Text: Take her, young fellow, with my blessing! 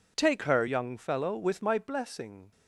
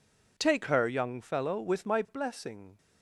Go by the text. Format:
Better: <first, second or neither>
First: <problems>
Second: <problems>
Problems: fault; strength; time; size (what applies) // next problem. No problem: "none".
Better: neither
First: none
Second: none